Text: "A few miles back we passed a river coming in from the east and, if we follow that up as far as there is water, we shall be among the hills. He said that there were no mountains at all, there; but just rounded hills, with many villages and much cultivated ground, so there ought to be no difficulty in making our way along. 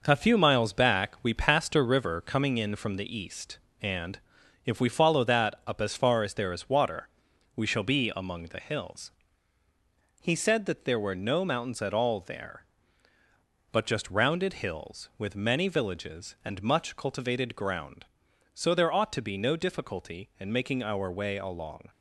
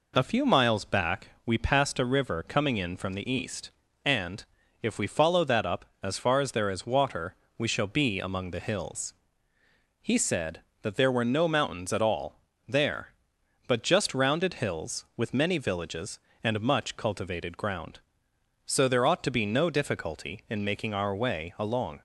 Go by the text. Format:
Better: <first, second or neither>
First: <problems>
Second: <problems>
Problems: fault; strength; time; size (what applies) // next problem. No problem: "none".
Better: second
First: gets quieter; noticeable; throughout; 6 dB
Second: none